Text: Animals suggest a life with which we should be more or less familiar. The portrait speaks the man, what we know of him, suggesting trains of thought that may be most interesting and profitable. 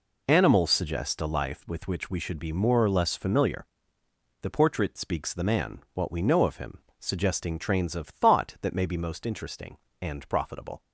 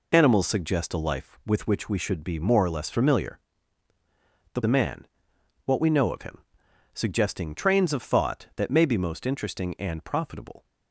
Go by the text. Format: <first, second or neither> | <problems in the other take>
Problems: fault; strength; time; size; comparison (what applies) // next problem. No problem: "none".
first | skips "portrait speaks the"; at 4.6 s